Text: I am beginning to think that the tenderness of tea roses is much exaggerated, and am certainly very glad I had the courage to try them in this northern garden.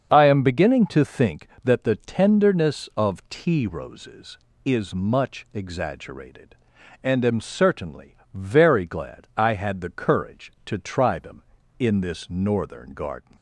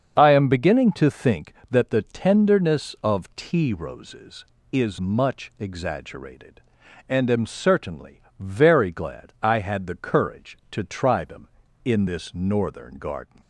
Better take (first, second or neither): neither